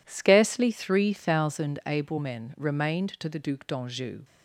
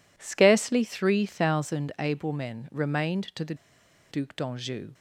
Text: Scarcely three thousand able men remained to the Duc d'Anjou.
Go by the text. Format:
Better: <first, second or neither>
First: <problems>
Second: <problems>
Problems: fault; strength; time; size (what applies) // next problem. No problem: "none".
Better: first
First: none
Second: pauses between "the" and "Duc"; noticeable; at 3.5 s; 0.56 s long